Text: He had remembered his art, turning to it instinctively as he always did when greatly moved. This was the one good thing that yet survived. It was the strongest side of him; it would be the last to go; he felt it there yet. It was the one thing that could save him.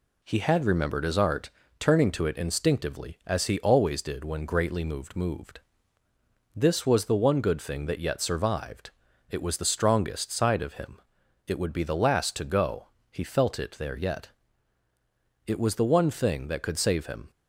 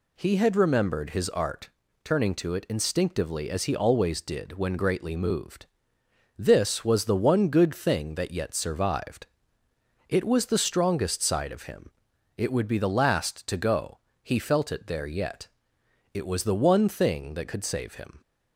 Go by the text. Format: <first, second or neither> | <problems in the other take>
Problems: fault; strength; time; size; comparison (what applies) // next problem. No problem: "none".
second | says "moved" twice; at 5.1 s